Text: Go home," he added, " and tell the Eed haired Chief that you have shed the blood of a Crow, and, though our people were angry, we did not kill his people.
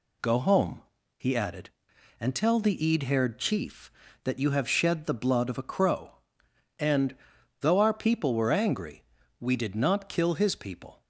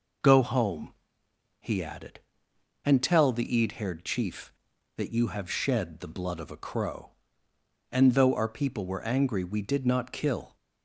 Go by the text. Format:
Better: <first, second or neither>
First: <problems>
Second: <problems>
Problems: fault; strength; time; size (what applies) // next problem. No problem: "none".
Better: first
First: none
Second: stops before "his people"; at 10.5 s